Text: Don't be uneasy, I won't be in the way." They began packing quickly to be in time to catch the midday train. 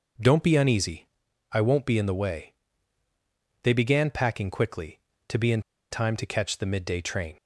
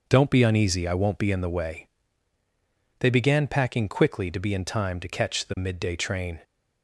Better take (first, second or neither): second